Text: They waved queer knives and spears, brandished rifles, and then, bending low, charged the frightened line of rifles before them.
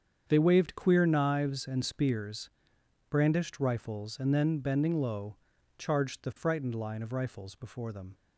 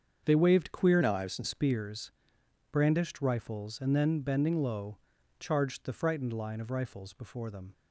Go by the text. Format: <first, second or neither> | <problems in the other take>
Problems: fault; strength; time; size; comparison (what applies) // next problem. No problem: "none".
first | starts louder than the rest; until 1.2 s; 7 dB; strong in the first // changes voice from "knives" to "and"; from 1.0 to 1.4 s; 0.4 s long